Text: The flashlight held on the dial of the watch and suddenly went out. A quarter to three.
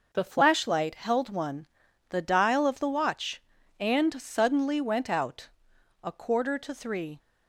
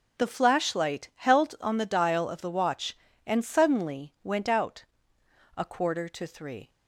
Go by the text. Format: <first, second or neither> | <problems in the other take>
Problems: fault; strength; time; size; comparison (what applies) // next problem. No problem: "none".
second | says "one" for "on"; at 1.3 s